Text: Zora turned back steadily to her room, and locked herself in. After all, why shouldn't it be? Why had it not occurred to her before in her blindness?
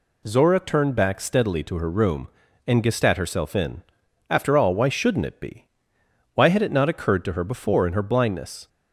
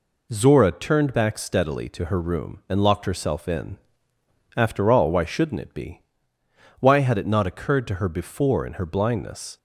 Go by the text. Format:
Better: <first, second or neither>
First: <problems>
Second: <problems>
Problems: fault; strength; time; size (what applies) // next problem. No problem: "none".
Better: second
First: says "gestat" for "locked"; at 2.8 s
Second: none